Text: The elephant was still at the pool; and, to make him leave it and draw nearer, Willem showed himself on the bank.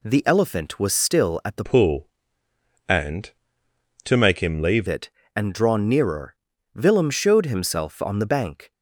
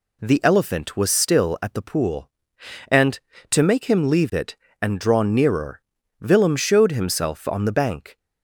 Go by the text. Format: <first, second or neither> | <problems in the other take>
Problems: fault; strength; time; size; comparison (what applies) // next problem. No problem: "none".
second | changes voice from "pool" to "leave"; from 1.6 to 4.8 s; 3.2 s long